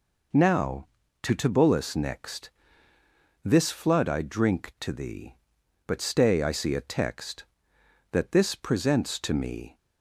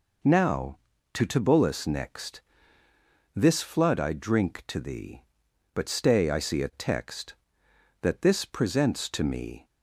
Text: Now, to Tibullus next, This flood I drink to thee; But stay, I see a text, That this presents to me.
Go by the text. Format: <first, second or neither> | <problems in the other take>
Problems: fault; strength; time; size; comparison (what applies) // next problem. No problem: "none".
neither | none